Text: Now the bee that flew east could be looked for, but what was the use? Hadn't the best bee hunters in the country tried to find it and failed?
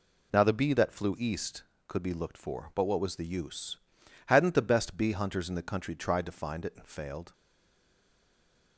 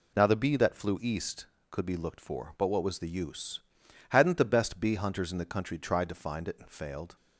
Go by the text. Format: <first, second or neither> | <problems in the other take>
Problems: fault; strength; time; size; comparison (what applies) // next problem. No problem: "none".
second | stays silent after the last word; noticeable; from 7.3 s on; 1.4 s long